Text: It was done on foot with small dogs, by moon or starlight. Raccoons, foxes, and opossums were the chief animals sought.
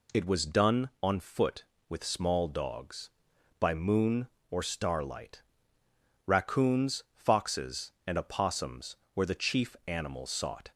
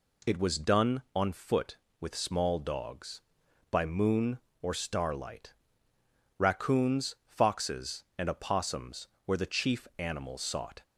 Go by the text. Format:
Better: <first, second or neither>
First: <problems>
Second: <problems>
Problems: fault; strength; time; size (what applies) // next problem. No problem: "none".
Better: neither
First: none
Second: none